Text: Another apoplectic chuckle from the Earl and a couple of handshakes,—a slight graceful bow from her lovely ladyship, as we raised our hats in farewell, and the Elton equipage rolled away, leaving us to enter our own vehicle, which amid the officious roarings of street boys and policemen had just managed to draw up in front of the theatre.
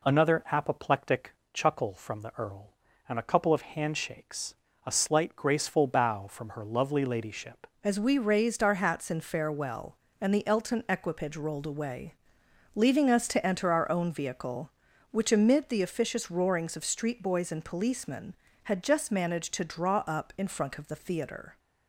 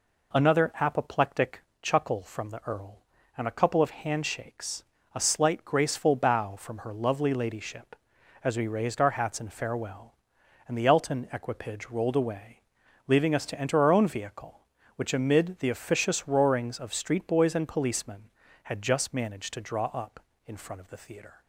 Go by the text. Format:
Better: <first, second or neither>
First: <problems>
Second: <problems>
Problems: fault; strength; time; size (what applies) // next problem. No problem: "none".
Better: second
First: pauses between "apoplectic" and "chuckle"; slight; at 1.3 s; 0.22 s long // changes voice at "as"; from 7.8 s on; 13.7 s long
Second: pauses between "apoplectic" and "chuckle"; slight; at 1.5 s; 0.22 s long